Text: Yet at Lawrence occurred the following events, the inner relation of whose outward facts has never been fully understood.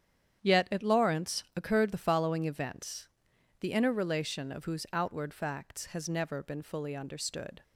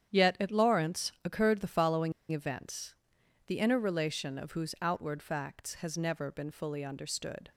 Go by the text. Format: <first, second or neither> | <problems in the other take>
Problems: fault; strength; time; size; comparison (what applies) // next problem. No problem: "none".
first | starts louder than the rest; strong; until 1.2 s; 9 dB; strong in the first // pauses between "following" and "events"; slight; at 2.1 s; 0.18 s long